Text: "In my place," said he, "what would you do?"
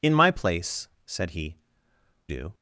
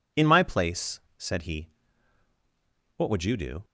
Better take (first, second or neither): second